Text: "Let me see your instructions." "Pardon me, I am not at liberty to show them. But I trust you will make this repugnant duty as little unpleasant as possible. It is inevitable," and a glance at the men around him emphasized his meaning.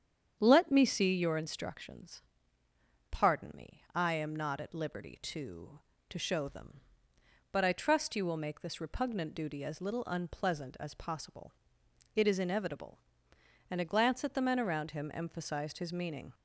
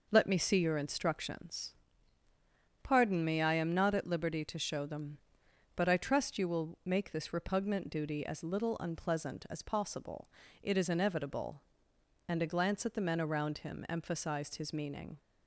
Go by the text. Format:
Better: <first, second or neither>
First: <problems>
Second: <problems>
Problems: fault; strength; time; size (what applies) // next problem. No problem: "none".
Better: second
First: starts louder than the rest; strong; until 1.4 s; 8 dB // says "to" twice; at 6.0 s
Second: none